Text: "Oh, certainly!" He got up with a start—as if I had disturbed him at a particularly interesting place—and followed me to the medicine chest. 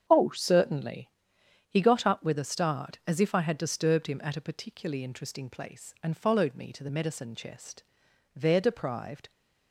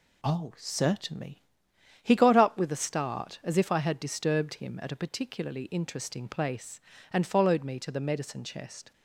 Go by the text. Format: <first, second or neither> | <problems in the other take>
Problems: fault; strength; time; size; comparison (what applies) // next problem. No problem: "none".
second | starts louder than the rest; strong; until 1.0 s; 7.5 dB // goes on to say "There deprived"; noticeable; from 8.3 s on; 0.94 s long